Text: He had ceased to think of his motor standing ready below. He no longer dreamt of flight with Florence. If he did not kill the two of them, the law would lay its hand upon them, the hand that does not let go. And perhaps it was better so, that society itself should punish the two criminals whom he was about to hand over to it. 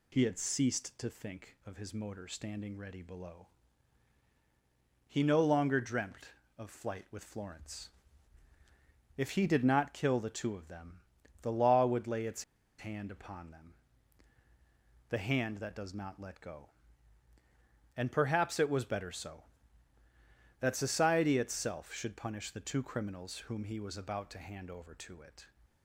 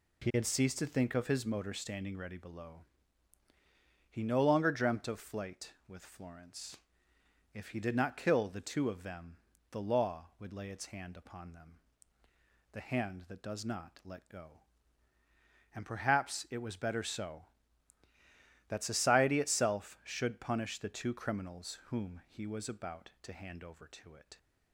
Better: second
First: pauses between "its" and "hand"; slight; at 12.4 s; 0.35 s long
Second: none

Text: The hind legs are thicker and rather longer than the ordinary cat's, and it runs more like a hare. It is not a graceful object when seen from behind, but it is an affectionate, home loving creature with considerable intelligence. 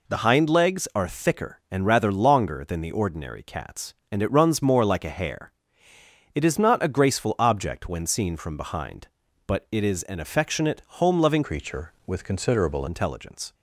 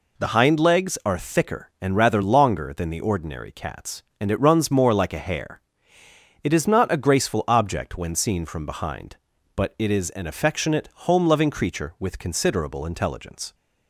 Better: second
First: changes voice from "creature" to "considerable"; from 11.4 to 12.8 s; 1.4 s long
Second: none

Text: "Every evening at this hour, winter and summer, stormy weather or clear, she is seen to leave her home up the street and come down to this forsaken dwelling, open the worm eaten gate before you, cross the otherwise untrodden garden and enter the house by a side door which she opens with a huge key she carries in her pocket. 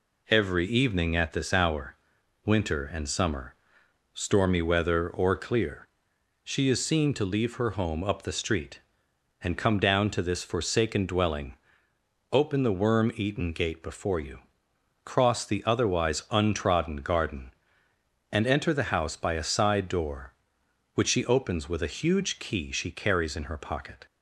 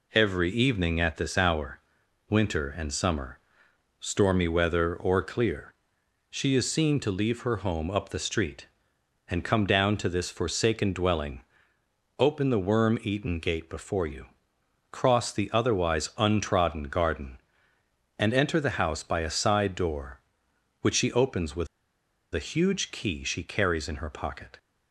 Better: first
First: none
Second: pauses between "with" and "a"; noticeable; at 21.6 s; 0.65 s long

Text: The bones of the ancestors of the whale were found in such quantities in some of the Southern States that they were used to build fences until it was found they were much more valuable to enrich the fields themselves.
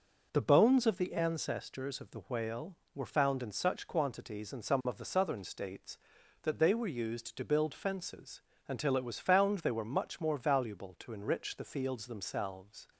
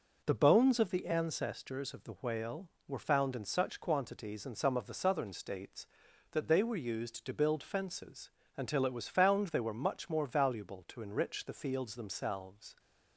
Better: neither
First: pauses between "fences" and "until"; slight; at 8.4 s; 0.26 s long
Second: pauses between "fences" and "until"; slight; at 8.3 s; 0.26 s long

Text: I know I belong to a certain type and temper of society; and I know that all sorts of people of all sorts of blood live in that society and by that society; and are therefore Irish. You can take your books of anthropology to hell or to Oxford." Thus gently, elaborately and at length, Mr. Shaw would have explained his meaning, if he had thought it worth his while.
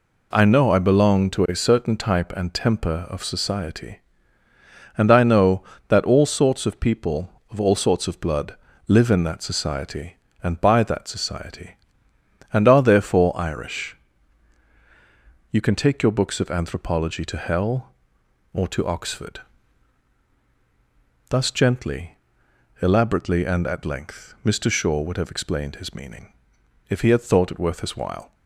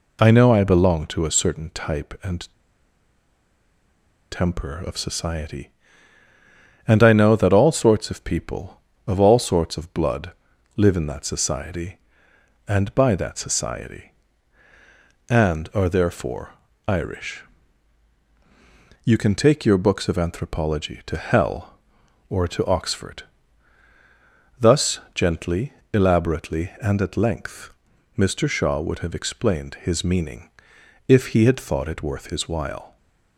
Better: first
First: pauses between "blood" and "live"; slight; at 8.5 s; 0.32 s long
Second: pauses between "and" and "temper"; strong; at 2.4 s; 1.8 s long // pauses between "blood" and "live"; at 10.3 s; 0.42 s long // pauses between "therefore" and "Irish"; slight; at 16.5 s; 0.36 s long // pauses between "Thus" and "gently"; slight; at 24.9 s; 0.16 s long

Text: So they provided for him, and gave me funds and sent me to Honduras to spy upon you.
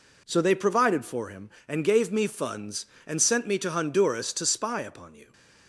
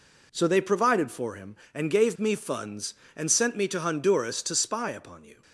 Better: neither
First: none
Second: none

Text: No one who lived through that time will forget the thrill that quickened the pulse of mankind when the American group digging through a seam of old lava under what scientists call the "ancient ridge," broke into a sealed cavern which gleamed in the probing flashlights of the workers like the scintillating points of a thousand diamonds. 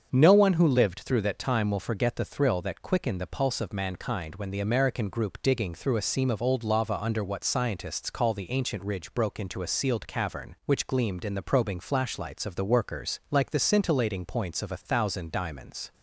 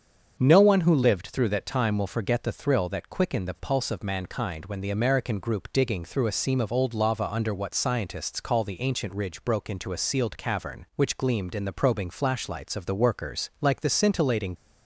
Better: first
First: starts louder than the rest; strong; until 1.1 s; 7 dB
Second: starts louder than the rest; strong; until 1.3 s; 7 dB // stops before "points of a thousand diamonds"; at 14.5 s

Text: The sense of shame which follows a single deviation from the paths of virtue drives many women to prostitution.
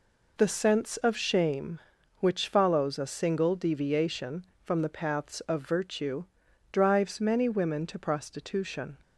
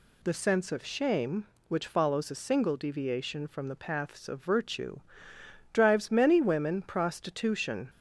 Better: first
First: pauses between "virtue" and "drives"; noticeable; at 6.2 s; 0.48 s long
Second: pauses between "virtue" and "drives"; noticeable; at 4.9 s; 0.72 s long // skips "to"; at 6.8 s

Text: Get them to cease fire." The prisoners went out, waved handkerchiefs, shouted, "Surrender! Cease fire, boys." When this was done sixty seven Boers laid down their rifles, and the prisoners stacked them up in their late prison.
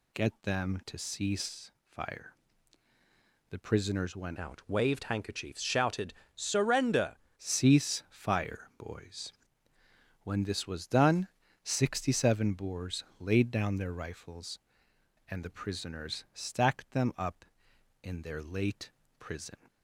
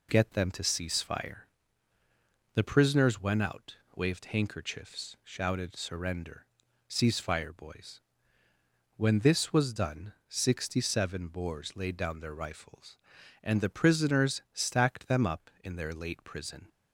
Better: second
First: pauses between "cease" and "fire"; slight; at 1.7 s; 0.18 s long // changes voice from "out" to "Surrender"; from 4.3 to 7.1 s; 2.8 s long // pauses between "done" and "sixty"; slight; at 11.2 s; 0.36 s long // pauses between "Boers" and "laid"; slight; at 13.0 s; 0.16 s long // pauses between "late" and "prison"; slight; at 18.9 s; 0.28 s long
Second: pauses between "done" and "sixty"; slight; at 10.1 s; 0.16 s long

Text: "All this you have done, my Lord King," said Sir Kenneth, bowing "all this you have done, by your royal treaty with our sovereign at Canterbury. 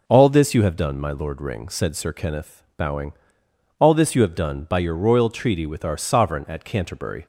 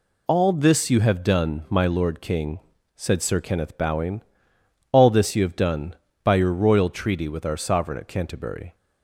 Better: second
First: says "Ring" for "King"; at 1.4 s // pauses between "bowing" and "all"; noticeable; at 3.1 s; 0.66 s long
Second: pauses between "bowing" and "all"; noticeable; at 4.2 s; 0.68 s long

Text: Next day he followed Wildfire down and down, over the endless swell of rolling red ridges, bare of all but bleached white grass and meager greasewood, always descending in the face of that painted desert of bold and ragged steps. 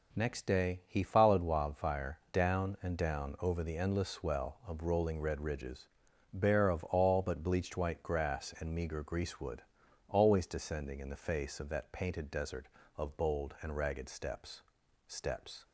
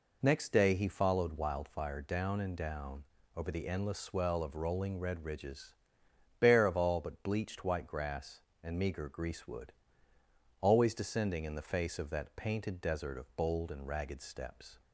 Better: second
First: says "steps" twice; at 15.0 s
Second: none

